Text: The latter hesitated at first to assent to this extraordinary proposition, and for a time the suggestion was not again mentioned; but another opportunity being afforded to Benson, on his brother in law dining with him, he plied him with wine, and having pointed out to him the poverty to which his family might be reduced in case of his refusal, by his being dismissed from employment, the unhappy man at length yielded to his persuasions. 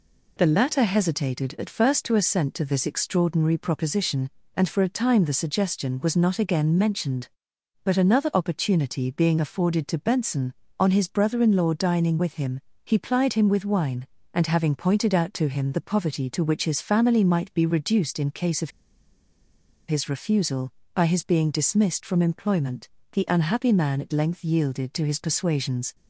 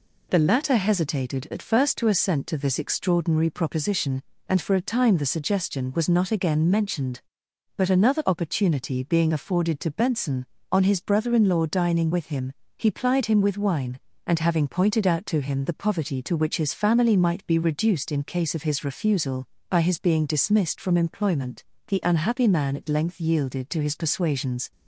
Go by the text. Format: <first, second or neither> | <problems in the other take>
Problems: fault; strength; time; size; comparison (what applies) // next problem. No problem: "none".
second | pauses between "of" and "his"; at 18.6 s; 1.1 s long